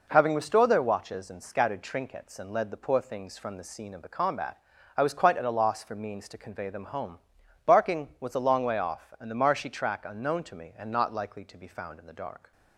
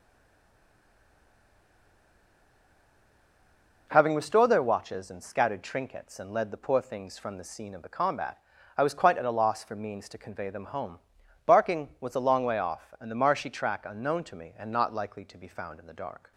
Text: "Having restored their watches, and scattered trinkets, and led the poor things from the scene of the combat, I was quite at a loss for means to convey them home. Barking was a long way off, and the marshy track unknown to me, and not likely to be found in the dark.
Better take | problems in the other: first | stays silent before the first word; strong; until 3.8 s; 3.8 s long

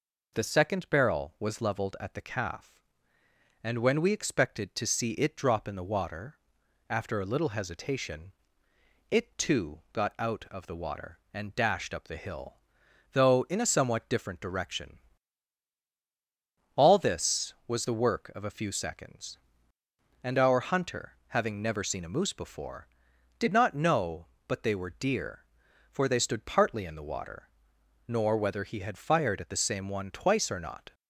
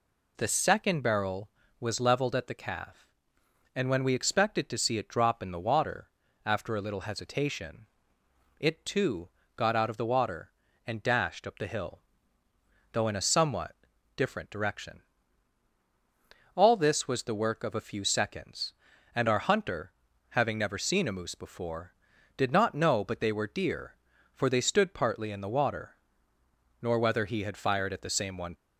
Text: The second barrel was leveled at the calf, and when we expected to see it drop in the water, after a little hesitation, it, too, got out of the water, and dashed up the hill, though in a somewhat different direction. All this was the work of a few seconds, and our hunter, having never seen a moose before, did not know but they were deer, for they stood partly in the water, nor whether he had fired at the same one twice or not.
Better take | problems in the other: first | pauses between "somewhat" and "different"; at 13.7 s; 0.40 s long // stops before "twice or not"; at 28.5 s

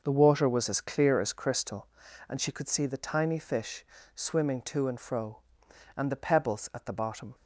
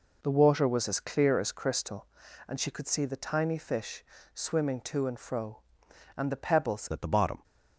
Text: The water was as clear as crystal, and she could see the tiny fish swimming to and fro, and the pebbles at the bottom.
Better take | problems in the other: first | pauses between "fish" and "swimming"; slight; at 4.0 s; 0.32 s long; slight in the first // changes voice at "at"; from 6.9 s on; 0.5 s long

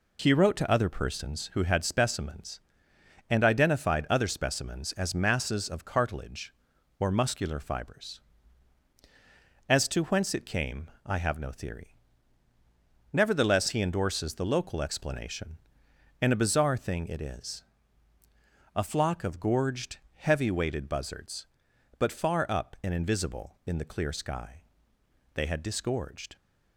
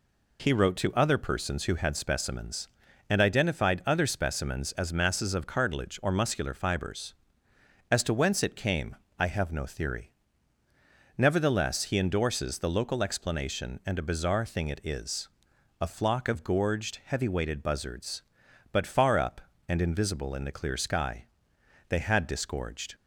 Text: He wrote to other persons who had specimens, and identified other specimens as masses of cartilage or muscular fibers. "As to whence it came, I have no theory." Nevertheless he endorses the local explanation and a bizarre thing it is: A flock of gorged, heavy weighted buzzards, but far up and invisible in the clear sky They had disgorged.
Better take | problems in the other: neither | pauses between "sky" and "They"; noticeable; the same in both

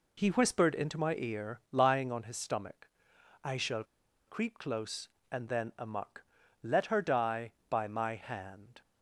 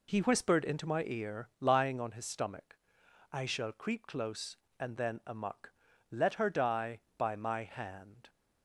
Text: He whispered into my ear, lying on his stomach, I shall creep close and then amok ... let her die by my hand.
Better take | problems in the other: second | pauses between "shall" and "creep"; at 3.8 s; 0.42 s long

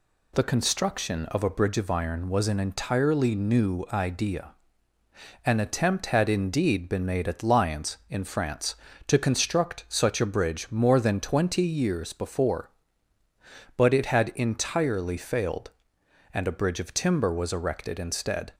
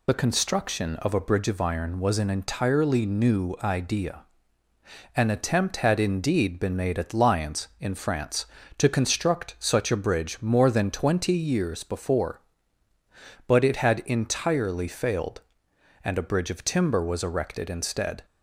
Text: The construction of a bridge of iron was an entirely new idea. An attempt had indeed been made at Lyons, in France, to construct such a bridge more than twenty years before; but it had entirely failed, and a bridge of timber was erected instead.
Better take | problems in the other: first | loses the start of "The"; at 0.0 s; 45 ms

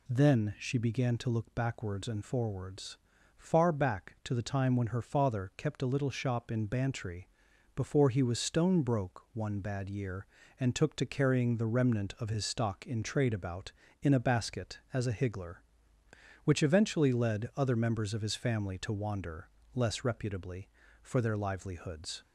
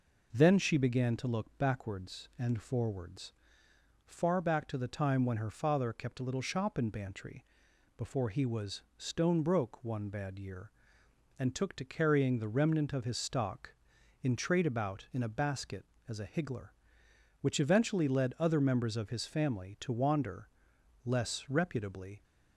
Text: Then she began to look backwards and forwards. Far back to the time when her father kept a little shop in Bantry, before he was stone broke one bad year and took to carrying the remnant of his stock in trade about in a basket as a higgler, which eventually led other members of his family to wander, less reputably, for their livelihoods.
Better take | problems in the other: first | pauses between "was" and "stone"; slight; at 8.8 s; 0.16 s long // stops before "for their livelihoods"; at 22.2 s

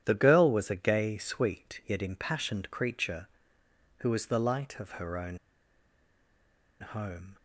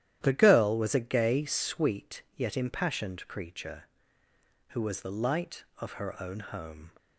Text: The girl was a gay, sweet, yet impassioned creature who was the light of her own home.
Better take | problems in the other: second | starts louder than the rest; strong; until 1.0 s; 10.5 dB; strong in the second // pauses between "own" and "home"; strong; at 5.3 s; 1.4 s long

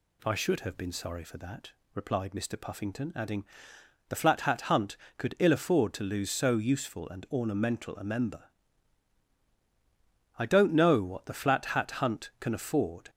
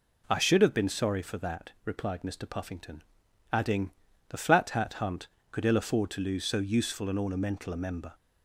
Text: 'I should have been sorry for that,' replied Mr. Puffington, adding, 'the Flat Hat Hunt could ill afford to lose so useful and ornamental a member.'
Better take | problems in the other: second | goes on to say "I don't know what the Flat Hat Hunt can afford"; strong; from 10.3 s on; 2.7 s long

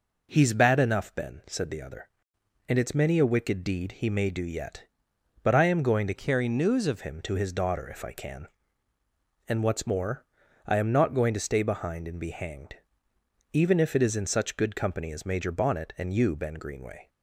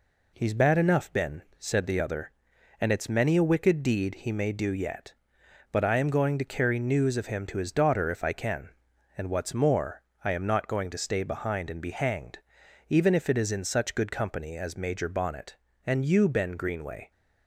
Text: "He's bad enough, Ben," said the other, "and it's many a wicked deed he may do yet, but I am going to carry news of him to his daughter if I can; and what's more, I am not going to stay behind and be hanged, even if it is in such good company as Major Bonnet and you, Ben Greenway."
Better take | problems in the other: second | changes voice from "carry" to "of"; from 6.1 to 6.9 s; 0.8 s long

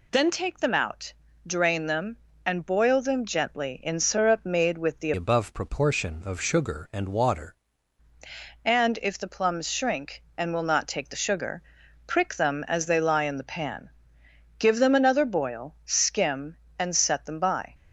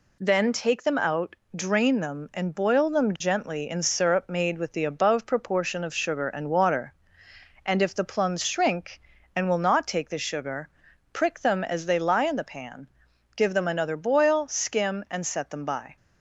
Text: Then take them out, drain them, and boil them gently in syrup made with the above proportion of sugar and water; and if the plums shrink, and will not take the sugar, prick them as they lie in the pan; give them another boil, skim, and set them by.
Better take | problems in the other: second | changes voice from "above" to "water"; from 5.1 to 7.5 s; 2.4 s long

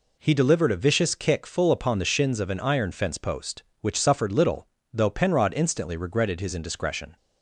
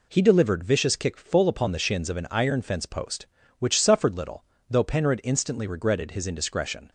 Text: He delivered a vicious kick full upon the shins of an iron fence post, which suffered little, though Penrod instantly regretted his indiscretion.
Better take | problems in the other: first | skips "a"; at 0.6 s

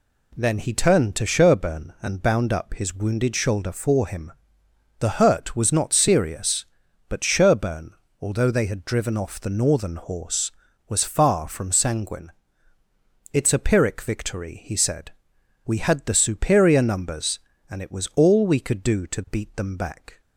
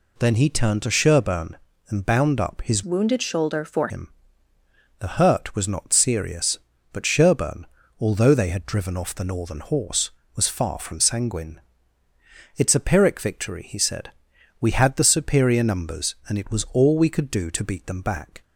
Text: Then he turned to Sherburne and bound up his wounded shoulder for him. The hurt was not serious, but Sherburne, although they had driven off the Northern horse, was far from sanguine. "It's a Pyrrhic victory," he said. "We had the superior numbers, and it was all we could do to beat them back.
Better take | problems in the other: first | changes voice from "wounded" to "for"; from 2.8 to 3.8 s; 1.0 s long

